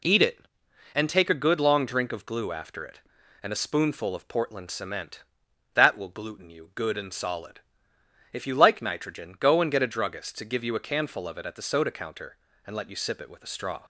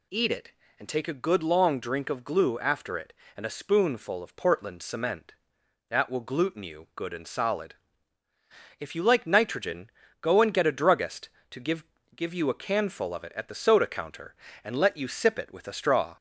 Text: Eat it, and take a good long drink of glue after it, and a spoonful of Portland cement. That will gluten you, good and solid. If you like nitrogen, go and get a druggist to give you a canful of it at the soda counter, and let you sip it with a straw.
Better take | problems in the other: first | says "give" twice; at 12.1 s

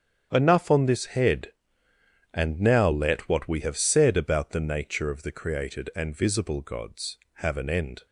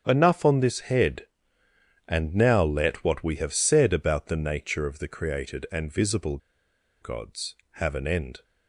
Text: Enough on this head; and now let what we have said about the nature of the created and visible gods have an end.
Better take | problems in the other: first | starts louder than the rest; strong; until 1.0 s; 8 dB; strong in the first // pauses between "visible" and "gods"; noticeable; at 6.3 s; 0.63 s long

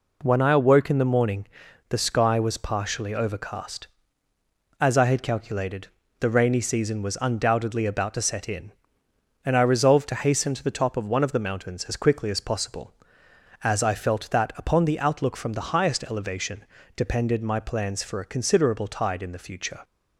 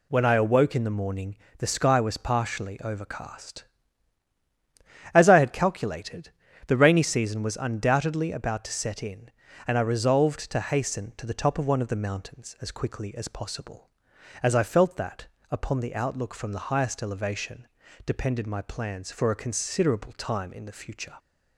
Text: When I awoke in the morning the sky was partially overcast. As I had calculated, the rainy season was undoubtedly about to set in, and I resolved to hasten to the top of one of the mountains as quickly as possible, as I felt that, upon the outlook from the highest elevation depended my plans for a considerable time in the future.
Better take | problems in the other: second | pauses between "morning" and "the"; at 1.4 s; 0.42 s long; slight in the second // pauses between "elevation" and "depended"; slight; at 16.6 s; 0.30 s long; also in the second // says "tide" for "time"; at 18.8 s

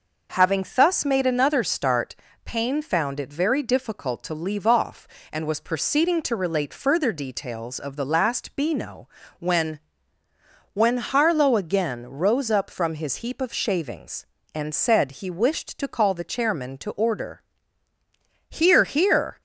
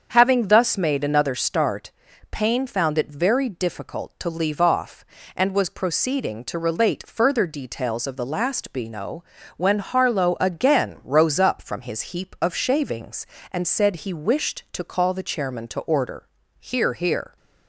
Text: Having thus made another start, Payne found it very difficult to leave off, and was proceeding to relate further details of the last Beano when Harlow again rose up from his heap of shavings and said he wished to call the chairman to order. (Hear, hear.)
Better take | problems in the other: second | starts louder than the rest; noticeable; until 1.4 s; 6 dB; also in the second // pauses between "Beano" and "when"; slight; at 9.0 s; 0.32 s long; slight in the second // says "when" twice; at 10.7 s

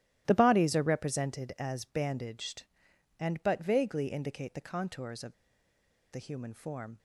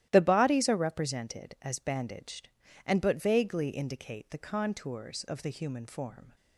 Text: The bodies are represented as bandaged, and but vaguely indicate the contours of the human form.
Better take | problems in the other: second | starts louder than the rest; strong; until 1.2 s; 14 dB; strong in the second // pauses between "of" and "the"; noticeable; at 5.3 s; 0.78 s long

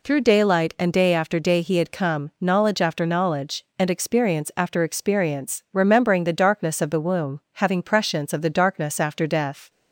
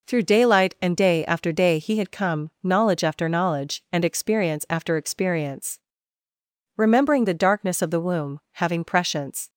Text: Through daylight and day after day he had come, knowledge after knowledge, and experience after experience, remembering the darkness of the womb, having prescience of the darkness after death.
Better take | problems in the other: first | stops before "of the darkness after death"; at 9.4 s

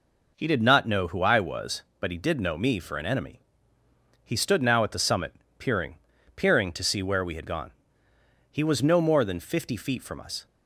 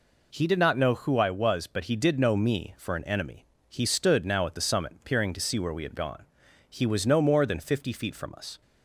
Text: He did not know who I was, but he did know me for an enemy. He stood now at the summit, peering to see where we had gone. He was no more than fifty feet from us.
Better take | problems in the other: second | says "peering" twice; at 6.3 s

